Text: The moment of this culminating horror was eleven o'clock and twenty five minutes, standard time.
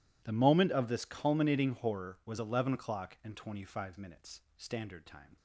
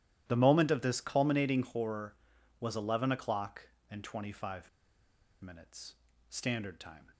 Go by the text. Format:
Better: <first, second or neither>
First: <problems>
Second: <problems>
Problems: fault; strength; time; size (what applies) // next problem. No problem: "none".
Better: first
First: none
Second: starts louder than the rest; strong; until 1.2 s; 12.5 dB // pauses between "five" and "minutes"; noticeable; at 4.6 s; 0.76 s long